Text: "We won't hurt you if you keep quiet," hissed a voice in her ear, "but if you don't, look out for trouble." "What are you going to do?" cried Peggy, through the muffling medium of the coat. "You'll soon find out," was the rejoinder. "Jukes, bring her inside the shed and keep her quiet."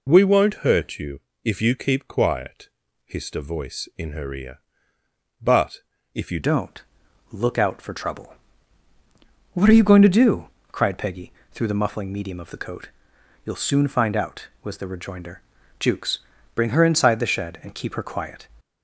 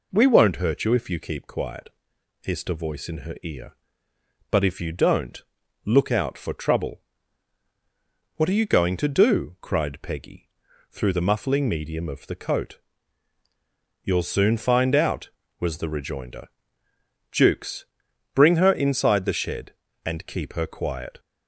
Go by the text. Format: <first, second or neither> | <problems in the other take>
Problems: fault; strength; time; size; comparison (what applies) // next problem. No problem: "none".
second | pauses between "you" and "if"; slight; at 1.1 s; 0.24 s long // pauses between "but" and "if"; slight; at 5.8 s; 0.32 s long // changes voice at "don't"; from 6.4 s on; 12.0 s long